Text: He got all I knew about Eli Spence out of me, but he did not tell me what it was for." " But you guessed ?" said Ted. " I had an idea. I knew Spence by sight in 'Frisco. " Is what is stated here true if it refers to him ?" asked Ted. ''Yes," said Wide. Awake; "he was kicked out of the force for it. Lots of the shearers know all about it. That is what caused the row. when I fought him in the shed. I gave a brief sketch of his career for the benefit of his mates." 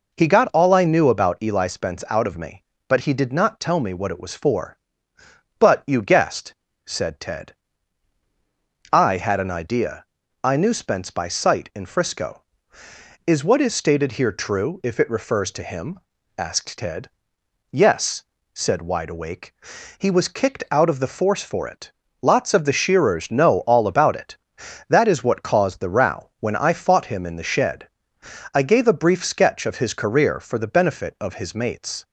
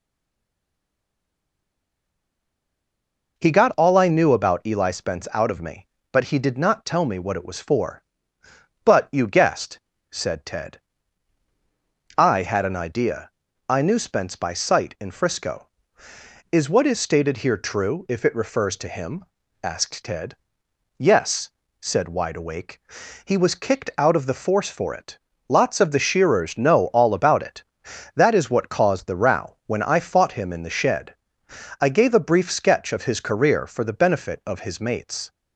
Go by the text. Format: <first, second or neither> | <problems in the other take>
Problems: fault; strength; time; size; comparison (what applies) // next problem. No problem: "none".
first | stays silent before the first word; strong; until 3.3 s; 3.3 s long